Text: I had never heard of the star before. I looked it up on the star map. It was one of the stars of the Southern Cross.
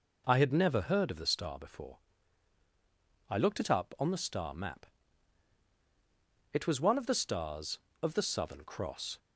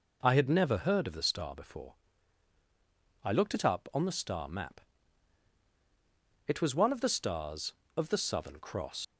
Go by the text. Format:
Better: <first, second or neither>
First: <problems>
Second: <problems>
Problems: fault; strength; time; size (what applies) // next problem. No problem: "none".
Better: first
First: none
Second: leaves "Cross" unfinished; at 9.0 s; 85 ms